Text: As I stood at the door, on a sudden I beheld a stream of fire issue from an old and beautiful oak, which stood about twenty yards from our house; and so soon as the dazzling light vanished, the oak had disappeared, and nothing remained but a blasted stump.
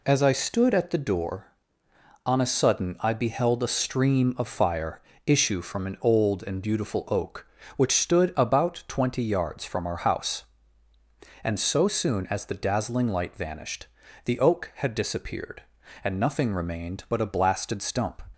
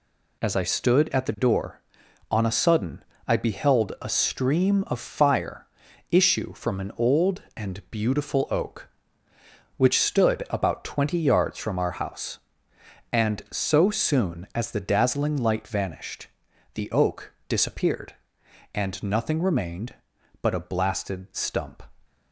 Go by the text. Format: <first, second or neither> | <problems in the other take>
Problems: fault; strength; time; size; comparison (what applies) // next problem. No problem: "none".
first | pauses between "sudden" and "I"; slight; at 3.0 s; 0.24 s long // pauses between "fire" and "issue"; at 5.6 s; 0.44 s long; slight in the first // skips "had"; at 17.3 s